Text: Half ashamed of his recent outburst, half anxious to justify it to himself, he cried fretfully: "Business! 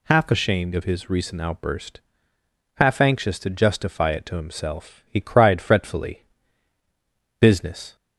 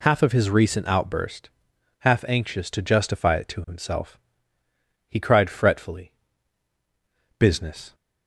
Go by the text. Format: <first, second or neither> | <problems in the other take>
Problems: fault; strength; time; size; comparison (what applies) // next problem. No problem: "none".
first | skips "ashamed"; at 0.2 s